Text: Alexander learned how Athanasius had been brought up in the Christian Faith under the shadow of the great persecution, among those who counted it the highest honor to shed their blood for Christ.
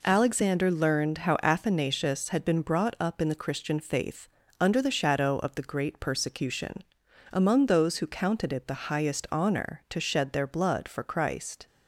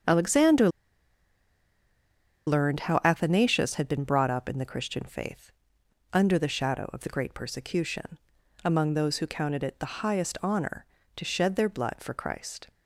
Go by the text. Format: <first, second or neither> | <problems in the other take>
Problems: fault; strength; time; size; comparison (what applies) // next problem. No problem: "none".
first | starts louder than the rest; until 2.8 s; 7 dB // pauses between "Alexander" and "learned"; strong; at 0.6 s; 1.7 s long // pauses between "Faith" and "under"; noticeable; at 5.5 s; 0.62 s long; slight in the first